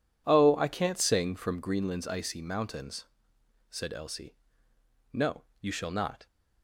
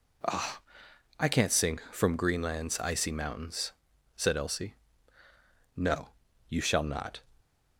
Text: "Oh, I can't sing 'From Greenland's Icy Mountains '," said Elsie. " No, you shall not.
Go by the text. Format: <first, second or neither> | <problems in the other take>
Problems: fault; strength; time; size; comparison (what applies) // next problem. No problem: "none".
second | starts louder than the rest; strong; until 1.7 s; 10.5 dB